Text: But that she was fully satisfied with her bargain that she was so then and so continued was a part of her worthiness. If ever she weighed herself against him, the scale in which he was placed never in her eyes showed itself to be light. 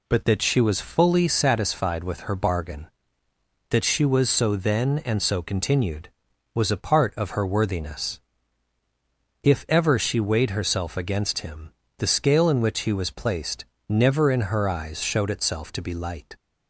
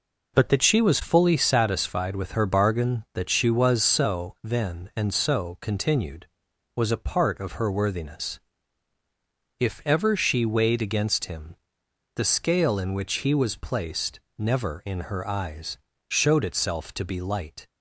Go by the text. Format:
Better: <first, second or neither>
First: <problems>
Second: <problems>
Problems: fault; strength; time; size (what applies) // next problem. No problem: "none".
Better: first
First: pauses between "placed" and "never"; slight; at 13.6 s; 0.24 s long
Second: skips "herself"; at 10.8 s // pauses between "placed" and "never"; slight; at 14.1 s; 0.18 s long // pauses between "eyes" and "showed"; slight; at 15.7 s; 0.32 s long